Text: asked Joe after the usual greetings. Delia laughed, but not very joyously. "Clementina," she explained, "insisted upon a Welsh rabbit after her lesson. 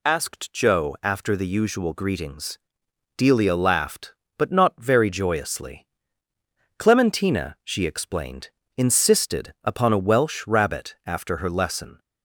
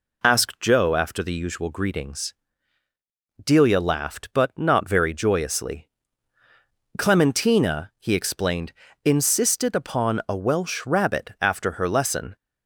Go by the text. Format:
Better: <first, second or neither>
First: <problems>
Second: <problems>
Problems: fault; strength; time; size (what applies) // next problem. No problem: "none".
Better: first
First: none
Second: says "he" for "she"; at 7.9 s